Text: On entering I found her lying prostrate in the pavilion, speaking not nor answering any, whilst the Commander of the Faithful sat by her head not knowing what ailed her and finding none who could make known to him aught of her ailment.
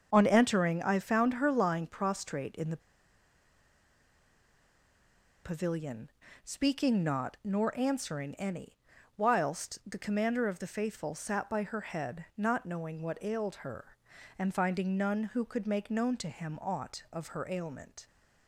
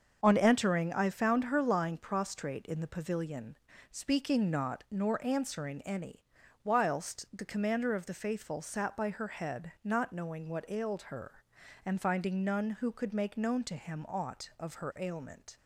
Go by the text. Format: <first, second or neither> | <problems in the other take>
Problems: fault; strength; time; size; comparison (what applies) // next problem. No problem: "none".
second | starts louder than the rest; until 1.1 s; 6.5 dB; also in the second // pauses between "the" and "pavilion"; strong; at 2.7 s; 2.6 s long